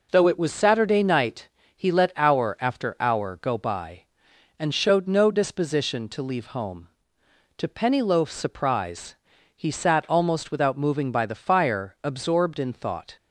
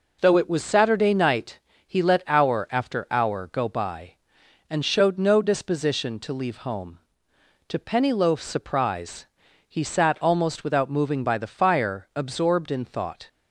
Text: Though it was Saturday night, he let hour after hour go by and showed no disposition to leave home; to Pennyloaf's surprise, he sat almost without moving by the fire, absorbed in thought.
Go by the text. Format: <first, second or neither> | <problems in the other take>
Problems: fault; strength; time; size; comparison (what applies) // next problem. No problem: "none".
neither | none